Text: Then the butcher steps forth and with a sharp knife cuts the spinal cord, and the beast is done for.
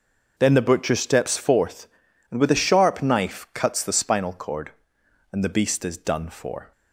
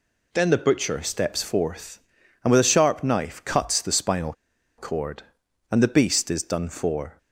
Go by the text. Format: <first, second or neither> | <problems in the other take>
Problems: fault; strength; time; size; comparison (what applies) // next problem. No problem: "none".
first | pauses between "spinal" and "cord"; at 4.3 s; 0.45 s long